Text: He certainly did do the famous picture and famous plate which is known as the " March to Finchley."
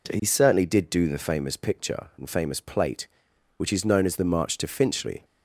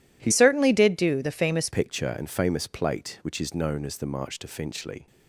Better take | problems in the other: first | changes voice from "certainly" to "famous"; from 0.3 to 1.6 s; 1.3 s long

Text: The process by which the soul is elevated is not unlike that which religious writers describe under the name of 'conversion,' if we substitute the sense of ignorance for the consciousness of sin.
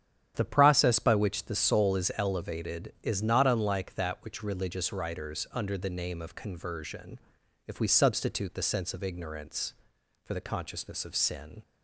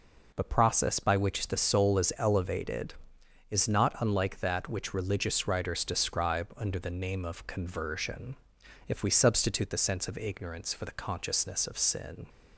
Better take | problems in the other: second | starts louder than the rest; strong; until 1.3 s; 9.5 dB // skips "describe"; at 5.5 s

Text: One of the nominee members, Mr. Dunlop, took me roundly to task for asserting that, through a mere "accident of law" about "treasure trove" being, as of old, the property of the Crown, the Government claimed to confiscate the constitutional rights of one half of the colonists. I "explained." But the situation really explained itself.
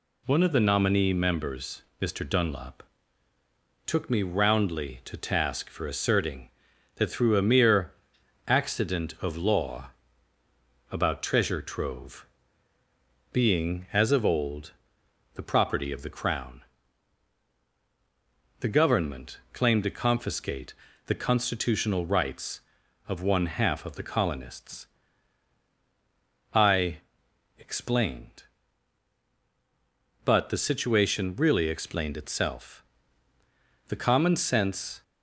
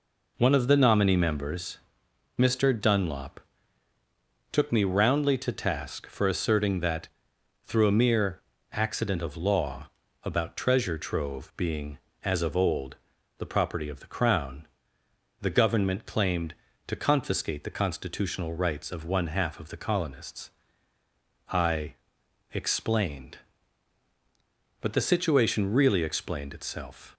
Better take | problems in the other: second | pauses between "mere" and "accident"; noticeable; at 7.9 s; 0.54 s long; slight in the second // pauses between "law" and "about"; at 9.9 s; 1.0 s long; also in the second // pauses between "trove" and "being"; at 12.2 s; 1.0 s long // pauses between "confiscate" and "the"; slight; at 20.7 s; 0.32 s long // pauses between "I" and "explained"; noticeable; at 27.0 s; 0.58 s long; noticeable in the second // goes on to say "The common sense"; noticeable; from 33.8 s on; 1.1 s long

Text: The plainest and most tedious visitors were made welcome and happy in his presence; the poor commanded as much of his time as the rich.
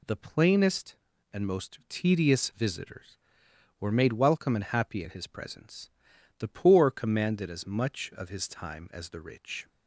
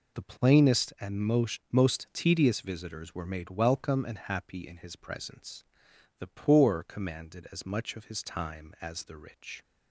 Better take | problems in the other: first | says "most" twice; at 1.7 s

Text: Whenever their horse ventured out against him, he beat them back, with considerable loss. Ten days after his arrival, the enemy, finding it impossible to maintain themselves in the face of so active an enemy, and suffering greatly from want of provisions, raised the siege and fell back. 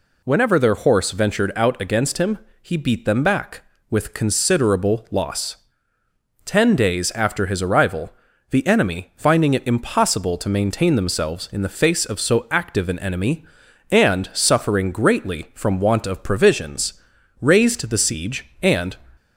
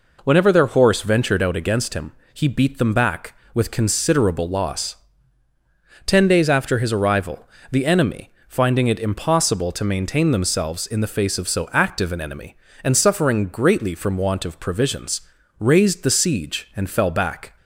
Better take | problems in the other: second | stops before "fell back"; at 19.1 s

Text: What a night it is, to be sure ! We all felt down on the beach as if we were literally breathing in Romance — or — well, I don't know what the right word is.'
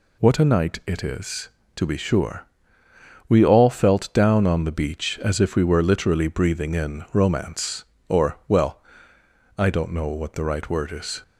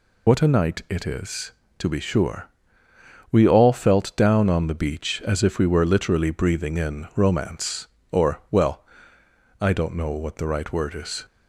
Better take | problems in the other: first | loses the start of "What"; at 0.2 s; 45 ms

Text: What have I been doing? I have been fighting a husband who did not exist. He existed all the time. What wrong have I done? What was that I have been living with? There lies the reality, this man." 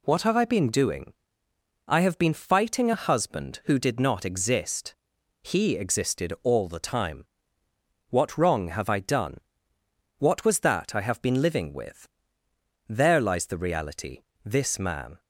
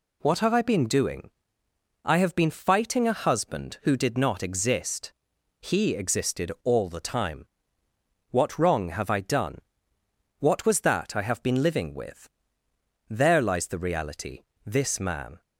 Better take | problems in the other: neither | none

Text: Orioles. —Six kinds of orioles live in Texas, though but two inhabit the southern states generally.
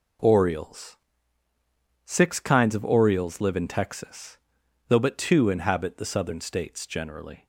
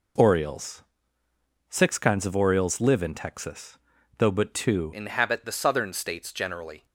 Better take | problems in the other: first | changes voice at "inhabit"; from 4.9 s on; 1.9 s long

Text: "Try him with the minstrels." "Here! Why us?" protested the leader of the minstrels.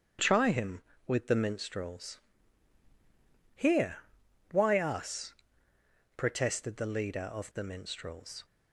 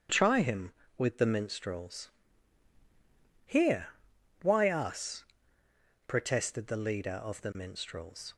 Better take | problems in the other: neither | starts louder than the rest; strong; the same in both

